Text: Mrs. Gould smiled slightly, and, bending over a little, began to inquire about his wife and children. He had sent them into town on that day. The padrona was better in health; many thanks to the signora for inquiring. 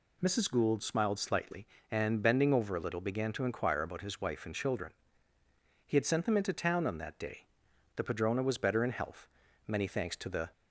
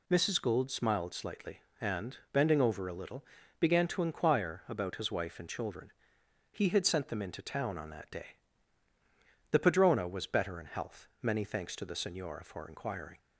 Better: second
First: stops before "signora for inquiring"; at 10.5 s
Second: none

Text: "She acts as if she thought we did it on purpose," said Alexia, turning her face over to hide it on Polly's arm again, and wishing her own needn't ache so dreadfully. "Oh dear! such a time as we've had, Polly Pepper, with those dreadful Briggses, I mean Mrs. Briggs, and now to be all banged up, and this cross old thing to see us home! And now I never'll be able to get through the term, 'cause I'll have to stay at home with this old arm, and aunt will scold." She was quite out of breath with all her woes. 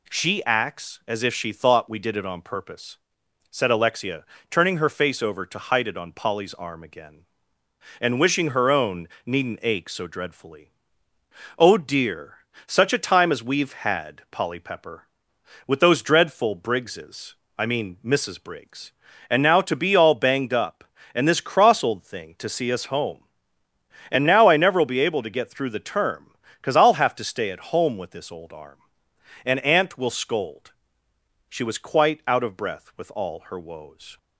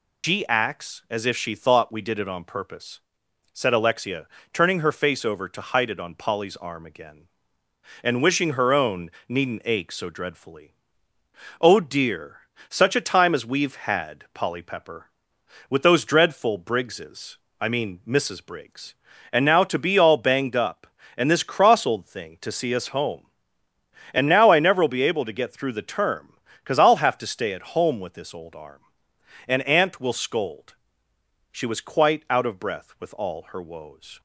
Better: first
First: pauses between "own" and "needn't"; slight; at 9.0 s; 0.18 s long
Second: loses the start of "She"; at 0.2 s; 140 ms // pauses between "own" and "needn't"; slight; at 9.0 s; 0.18 s long

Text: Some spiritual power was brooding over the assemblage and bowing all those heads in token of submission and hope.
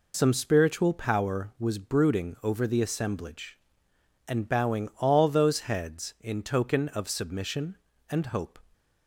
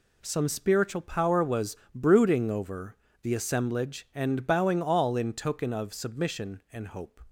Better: first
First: none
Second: pauses between "was" and "brooding"; slight; at 1.7 s; 0.20 s long // pauses between "over" and "the"; slight; at 2.9 s; 0.30 s long // skips "those heads"; at 5.1 s

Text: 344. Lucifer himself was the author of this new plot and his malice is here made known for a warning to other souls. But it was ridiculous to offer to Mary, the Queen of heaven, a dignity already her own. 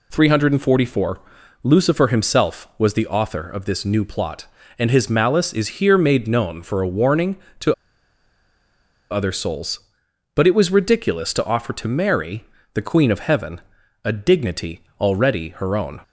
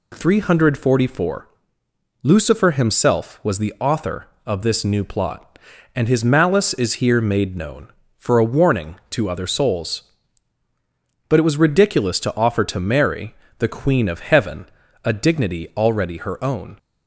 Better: second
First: pauses between "to" and "other"; strong; at 7.7 s; 1.3 s long // pauses between "dignity" and "already"; slight; at 14.8 s; 0.18 s long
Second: none

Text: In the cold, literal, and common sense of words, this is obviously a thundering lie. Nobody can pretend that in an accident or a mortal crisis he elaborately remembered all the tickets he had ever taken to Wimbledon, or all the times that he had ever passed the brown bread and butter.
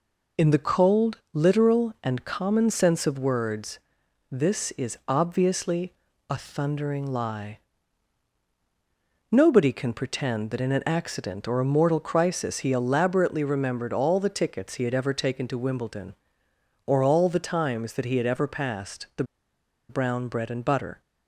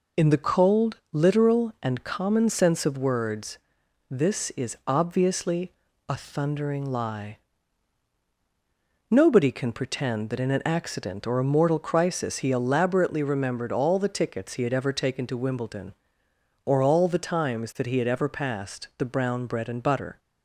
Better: second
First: pauses between "obviously" and "a"; at 5.9 s; 0.38 s long // pauses between "the" and "brown"; noticeable; at 19.2 s; 0.66 s long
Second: pauses between "obviously" and "a"; at 5.7 s; 0.38 s long

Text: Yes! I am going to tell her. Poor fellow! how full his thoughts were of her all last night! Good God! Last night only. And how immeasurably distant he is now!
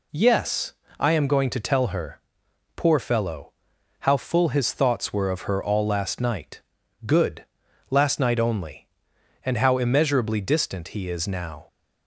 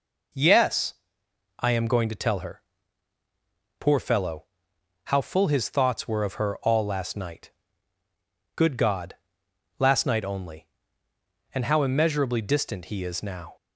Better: second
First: skips "God"; at 7.6 s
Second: none

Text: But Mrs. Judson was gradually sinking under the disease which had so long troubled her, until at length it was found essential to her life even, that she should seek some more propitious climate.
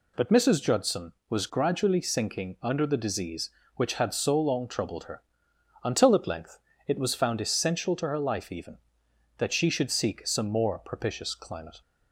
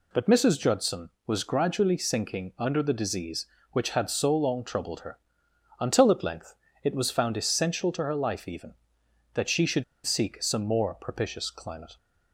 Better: first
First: pauses between "length" and "it"; slight; at 6.5 s; 0.28 s long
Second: pauses between "length" and "it"; slight; at 6.5 s; 0.28 s long // pauses between "should" and "seek"; slight; at 9.8 s; 0.22 s long

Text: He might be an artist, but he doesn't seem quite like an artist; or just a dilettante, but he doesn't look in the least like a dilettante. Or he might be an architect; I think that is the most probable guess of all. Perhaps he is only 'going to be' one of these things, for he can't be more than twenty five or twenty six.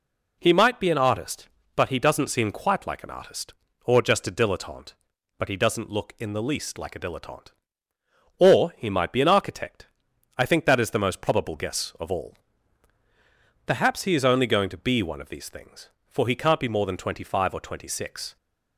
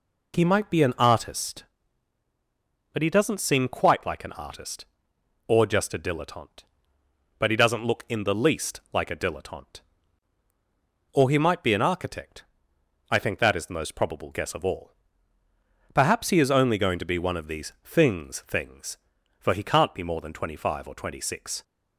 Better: first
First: none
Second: says "things" twice; at 18.4 s

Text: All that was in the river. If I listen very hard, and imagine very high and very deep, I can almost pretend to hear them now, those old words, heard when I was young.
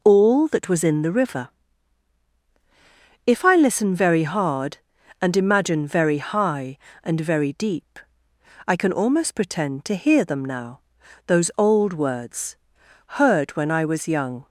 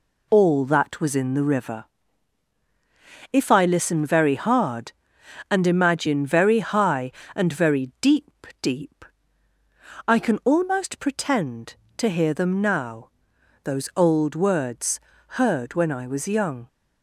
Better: first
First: none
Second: says "deep" twice; at 8.6 s

